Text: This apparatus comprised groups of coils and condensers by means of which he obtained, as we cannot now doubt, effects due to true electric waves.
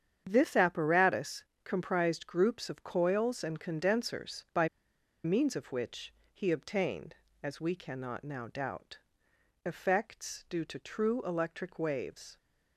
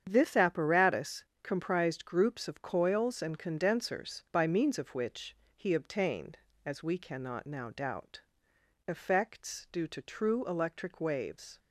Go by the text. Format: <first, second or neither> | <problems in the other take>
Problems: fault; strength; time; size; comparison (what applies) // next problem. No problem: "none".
second | starts louder than the rest; strong; until 1.2 s; 8 dB; strong in the second // pauses between "apparatus" and "comprised"; slight; at 1.4 s; 0.20 s long; slight in the second // pauses between "by" and "means"; noticeable; at 4.6 s; 0.56 s long // pauses between "which" and "he"; slight; at 6.1 s; 0.22 s long; slight in the second